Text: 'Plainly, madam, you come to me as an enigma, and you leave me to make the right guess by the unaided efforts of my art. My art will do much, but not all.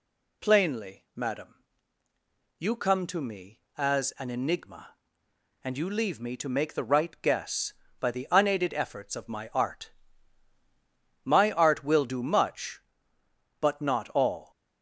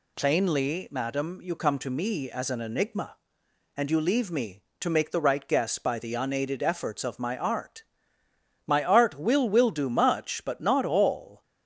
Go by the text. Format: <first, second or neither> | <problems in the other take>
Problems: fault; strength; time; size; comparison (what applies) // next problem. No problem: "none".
first | says "will" twice; at 9.4 s